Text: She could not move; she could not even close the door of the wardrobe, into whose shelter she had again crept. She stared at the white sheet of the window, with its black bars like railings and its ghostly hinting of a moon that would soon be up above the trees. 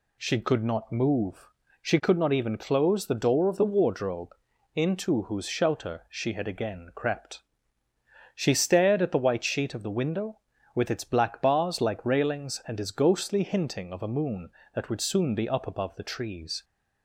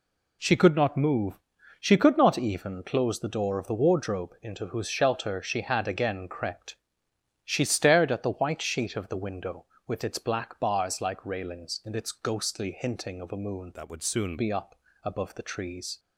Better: first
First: none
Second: changes voice from "that" to "soon"; from 13.7 to 14.3 s; 0.6 s long // pauses between "up" and "above"; slight; at 14.7 s; 0.28 s long

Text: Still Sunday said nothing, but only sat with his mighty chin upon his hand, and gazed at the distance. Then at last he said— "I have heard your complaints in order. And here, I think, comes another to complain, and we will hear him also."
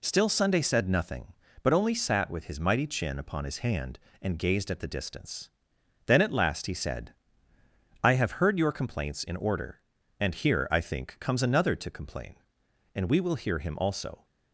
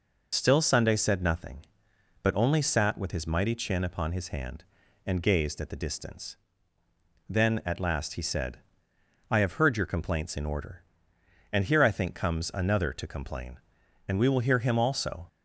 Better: first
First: none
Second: loses the start of "Still"; at 0.3 s; 50 ms

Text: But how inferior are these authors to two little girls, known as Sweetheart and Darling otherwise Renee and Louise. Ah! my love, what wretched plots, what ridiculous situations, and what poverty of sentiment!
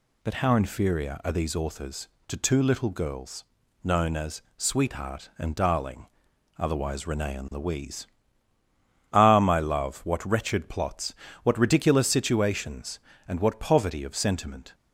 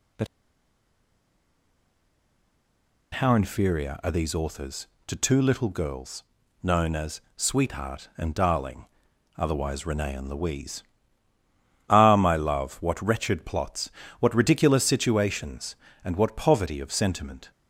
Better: first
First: pauses between "as" and "Sweetheart"; slight; at 4.4 s; 0.16 s long // pauses between "Darling" and "otherwise"; noticeable; at 6.0 s; 0.52 s long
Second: pauses between "But" and "how"; strong; at 0.2 s; 2.8 s long // pauses between "as" and "Sweetheart"; slight; at 7.2 s; 0.16 s long // pauses between "Darling" and "otherwise"; noticeable; at 8.8 s; 0.52 s long

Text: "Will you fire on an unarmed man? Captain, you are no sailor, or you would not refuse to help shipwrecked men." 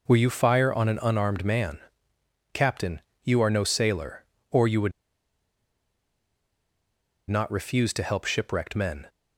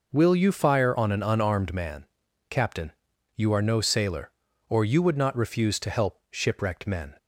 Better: second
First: pauses between "would" and "not"; strong; at 4.9 s; 2.3 s long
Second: none

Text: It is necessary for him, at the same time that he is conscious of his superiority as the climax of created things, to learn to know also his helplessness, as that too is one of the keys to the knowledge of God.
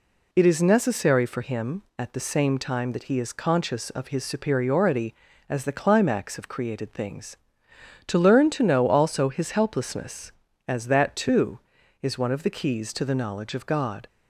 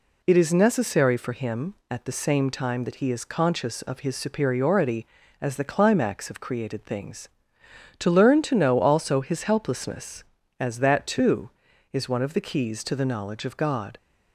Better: neither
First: none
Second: none

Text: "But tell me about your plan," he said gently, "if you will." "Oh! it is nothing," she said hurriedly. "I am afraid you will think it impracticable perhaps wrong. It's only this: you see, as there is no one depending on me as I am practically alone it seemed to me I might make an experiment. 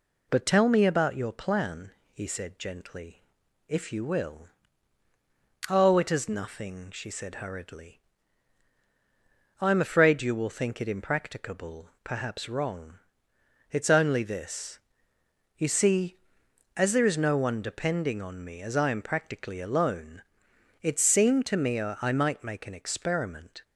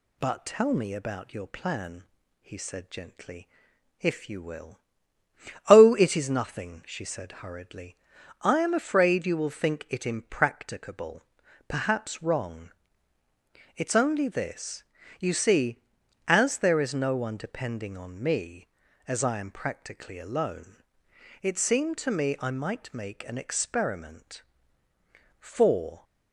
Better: first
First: pauses between "alone" and "it"; noticeable; at 20.2 s; 0.62 s long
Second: pauses between "impracticable" and "perhaps"; noticeable; at 11.2 s; 0.48 s long // pauses between "alone" and "it"; noticeable; at 20.8 s; 0.58 s long // goes on to say "Four"; noticeable; from 25.3 s on; 0.64 s long

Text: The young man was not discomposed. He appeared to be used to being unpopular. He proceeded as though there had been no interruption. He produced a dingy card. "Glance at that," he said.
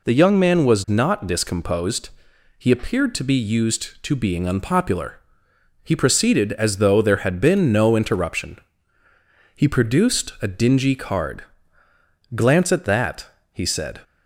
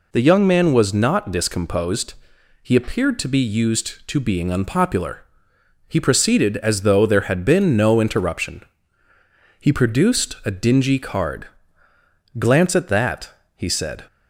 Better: neither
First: none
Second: none

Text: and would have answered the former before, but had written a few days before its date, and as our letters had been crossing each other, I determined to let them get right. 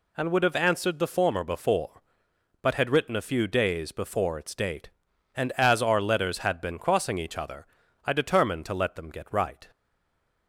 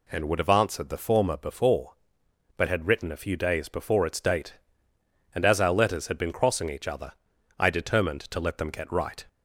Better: second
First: stays silent after the last word; slight; from 9.7 s on; 0.7 s long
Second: none

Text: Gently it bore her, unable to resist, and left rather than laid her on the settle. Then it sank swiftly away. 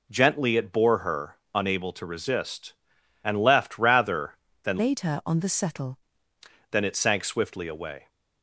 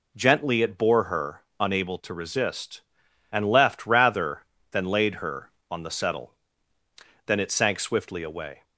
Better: second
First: changes voice from "laid" to "settle"; from 4.7 to 5.9 s; 1.2 s long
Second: none

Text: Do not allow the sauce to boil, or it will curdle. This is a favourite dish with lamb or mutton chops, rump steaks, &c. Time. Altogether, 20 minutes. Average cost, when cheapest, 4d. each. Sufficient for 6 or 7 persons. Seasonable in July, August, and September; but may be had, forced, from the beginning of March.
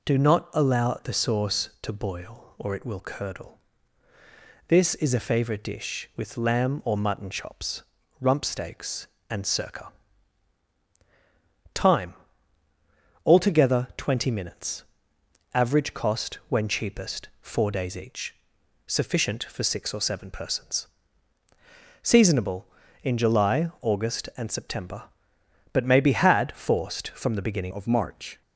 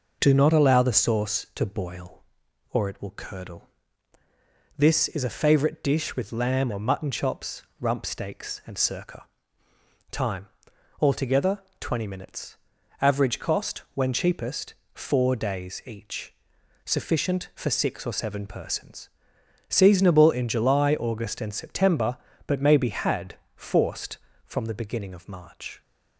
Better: second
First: changes voice at "of"; from 27.7 s on; 0.7 s long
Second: none

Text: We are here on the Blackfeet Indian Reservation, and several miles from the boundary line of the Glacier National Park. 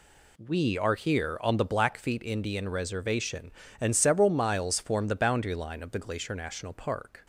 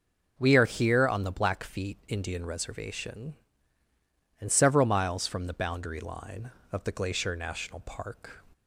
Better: second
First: says "form" for "from"; at 4.7 s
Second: none

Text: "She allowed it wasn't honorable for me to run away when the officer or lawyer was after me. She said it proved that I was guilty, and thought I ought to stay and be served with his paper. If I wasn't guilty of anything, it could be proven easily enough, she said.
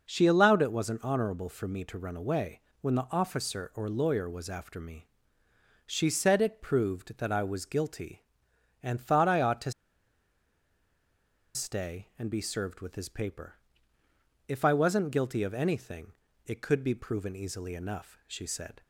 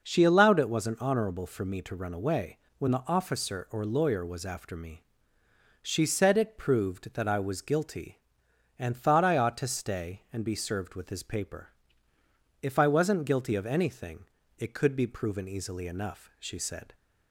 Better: second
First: pauses between "away" and "when"; slight; at 2.6 s; 0.20 s long // pauses between "to" and "stay"; strong; at 9.7 s; 1.8 s long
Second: pauses between "away" and "when"; slight; at 2.5 s; 0.20 s long

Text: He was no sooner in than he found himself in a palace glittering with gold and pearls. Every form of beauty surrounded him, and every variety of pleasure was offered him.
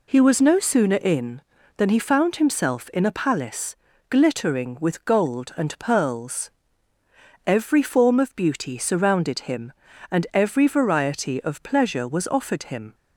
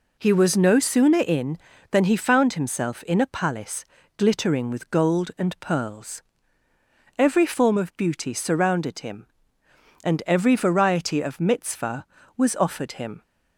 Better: first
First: pauses between "palace" and "glittering"; slight; at 3.7 s; 0.32 s long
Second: pauses between "palace" and "glittering"; slight; at 3.8 s; 0.32 s long // says "mitzvah" for "pleasure"; at 11.3 s

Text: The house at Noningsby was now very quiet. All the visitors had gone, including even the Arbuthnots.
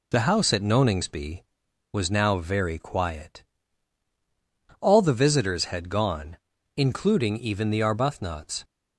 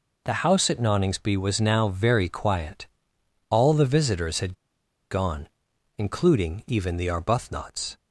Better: first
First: none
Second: pauses between "had" and "gone"; noticeable; at 4.5 s; 0.58 s long

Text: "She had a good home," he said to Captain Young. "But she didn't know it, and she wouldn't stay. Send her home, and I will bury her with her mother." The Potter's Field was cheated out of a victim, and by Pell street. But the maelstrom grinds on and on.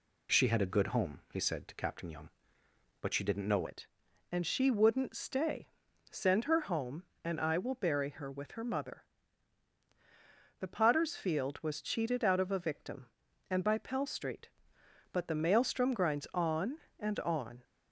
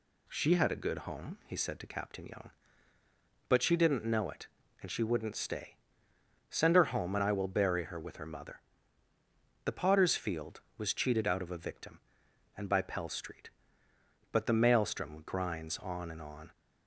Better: second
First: changes voice at "it"; from 3.6 s on; 14.0 s long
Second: none

